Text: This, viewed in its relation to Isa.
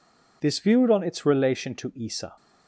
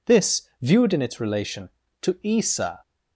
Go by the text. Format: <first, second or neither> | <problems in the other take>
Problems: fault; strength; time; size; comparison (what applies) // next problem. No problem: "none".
second | says "on" for "in"; at 0.8 s